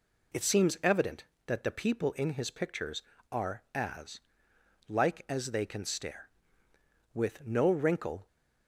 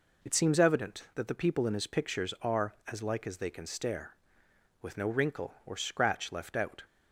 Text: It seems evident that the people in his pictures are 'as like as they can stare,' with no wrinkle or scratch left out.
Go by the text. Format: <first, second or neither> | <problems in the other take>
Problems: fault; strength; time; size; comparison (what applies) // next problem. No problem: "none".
second | pauses between "as" and "like"; noticeable; at 4.2 s; 0.68 s long // stops before "or scratch left out"; at 8.2 s